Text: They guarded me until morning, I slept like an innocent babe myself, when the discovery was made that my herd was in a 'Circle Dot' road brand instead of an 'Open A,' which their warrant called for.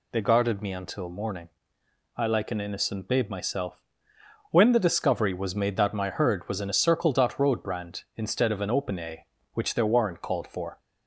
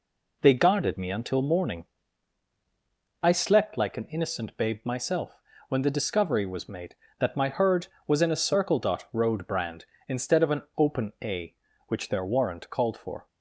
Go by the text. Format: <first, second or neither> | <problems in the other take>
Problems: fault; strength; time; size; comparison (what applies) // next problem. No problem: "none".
second | skips "slept"; at 2.2 s